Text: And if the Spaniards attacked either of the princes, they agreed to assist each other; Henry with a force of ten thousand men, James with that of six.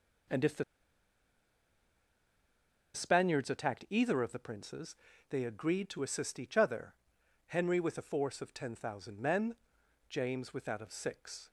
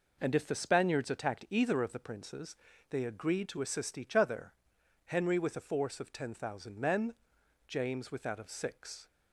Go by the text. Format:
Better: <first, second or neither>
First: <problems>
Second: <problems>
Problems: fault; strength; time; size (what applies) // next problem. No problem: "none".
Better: second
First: pauses between "the" and "Spaniards"; strong; at 0.6 s; 2.3 s long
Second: none